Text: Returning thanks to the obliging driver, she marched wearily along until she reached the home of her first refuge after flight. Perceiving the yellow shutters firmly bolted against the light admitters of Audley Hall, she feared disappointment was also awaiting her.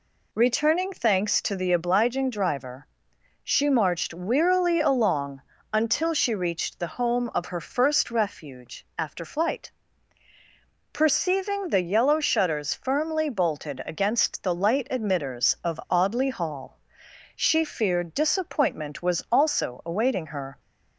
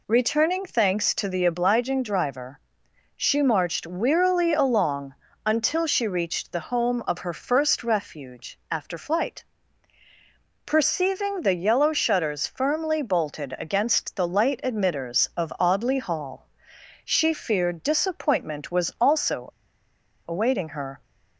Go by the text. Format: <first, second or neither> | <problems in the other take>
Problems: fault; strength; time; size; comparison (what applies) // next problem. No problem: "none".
first | pauses between "along" and "until"; slight; at 5.1 s; 0.32 s long; slight in the first // pauses between "also" and "awaiting"; noticeable; at 19.5 s; 0.77 s long